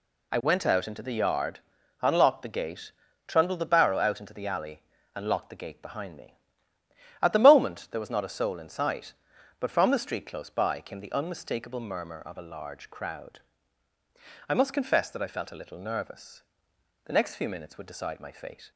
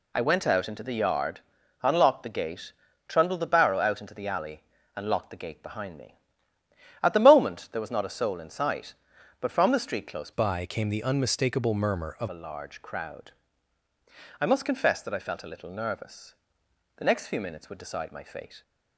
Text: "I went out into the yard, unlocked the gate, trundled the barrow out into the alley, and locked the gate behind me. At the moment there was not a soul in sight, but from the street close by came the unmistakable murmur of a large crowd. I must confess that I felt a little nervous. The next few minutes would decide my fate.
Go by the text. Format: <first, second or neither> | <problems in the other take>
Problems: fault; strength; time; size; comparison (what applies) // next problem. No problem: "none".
first | changes voice from "by" to "of"; from 10.3 to 12.2 s; 1.9 s long